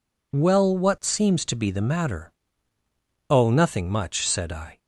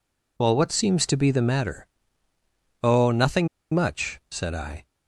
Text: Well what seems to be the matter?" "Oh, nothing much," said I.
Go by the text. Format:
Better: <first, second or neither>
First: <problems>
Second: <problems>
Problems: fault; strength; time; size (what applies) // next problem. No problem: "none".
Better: first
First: none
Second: pauses between "nothing" and "much"; slight; at 3.4 s; 0.26 s long